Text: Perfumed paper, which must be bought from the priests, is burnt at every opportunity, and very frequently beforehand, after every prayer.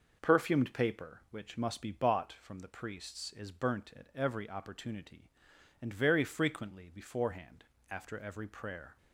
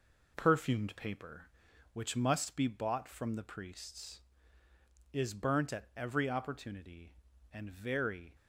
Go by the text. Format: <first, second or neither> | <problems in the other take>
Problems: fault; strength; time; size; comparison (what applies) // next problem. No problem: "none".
first | stops before "frequently beforehand after every prayer"; at 8.3 s